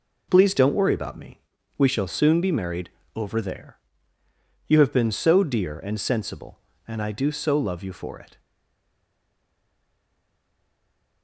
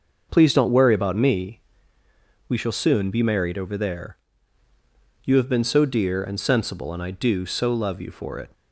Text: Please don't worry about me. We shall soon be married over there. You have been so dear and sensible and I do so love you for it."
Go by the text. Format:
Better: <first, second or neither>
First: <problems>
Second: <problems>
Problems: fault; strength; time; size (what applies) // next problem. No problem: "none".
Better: second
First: pauses between "married" and "over"; slight; at 2.8 s; 0.26 s long // stays silent after the last word; strong; from 8.3 s on; 2.9 s long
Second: none